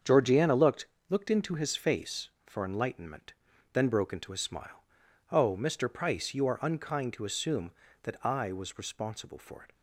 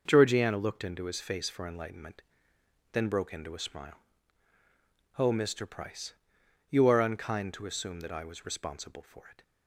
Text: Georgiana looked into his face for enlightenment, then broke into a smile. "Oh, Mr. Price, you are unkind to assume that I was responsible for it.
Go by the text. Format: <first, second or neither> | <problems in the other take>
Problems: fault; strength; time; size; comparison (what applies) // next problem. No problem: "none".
second | starts louder than the rest; strong; until 1.2 s; 7 dB // says "looked" twice; at 1.0 s